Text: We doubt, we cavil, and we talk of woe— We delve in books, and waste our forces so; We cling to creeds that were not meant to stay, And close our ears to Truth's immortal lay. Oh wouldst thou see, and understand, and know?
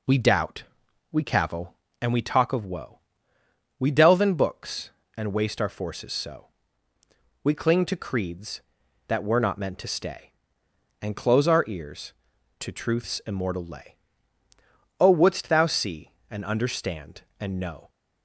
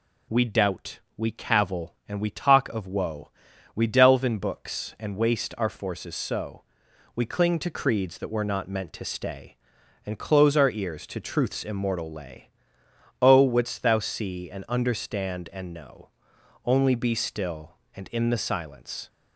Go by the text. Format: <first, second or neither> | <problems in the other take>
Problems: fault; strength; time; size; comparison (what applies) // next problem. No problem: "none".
first | goes on to say "Only be still and in the silence"; strong; from 16.6 s on; 2.4 s long